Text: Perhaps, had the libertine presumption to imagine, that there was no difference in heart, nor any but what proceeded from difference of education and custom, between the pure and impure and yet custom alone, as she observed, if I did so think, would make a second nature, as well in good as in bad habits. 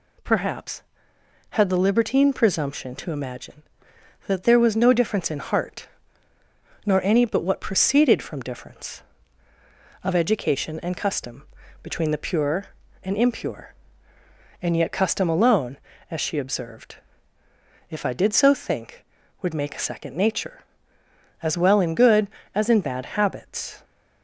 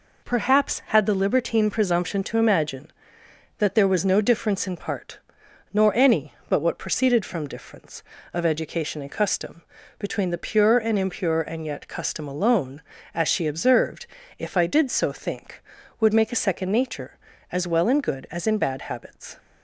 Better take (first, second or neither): first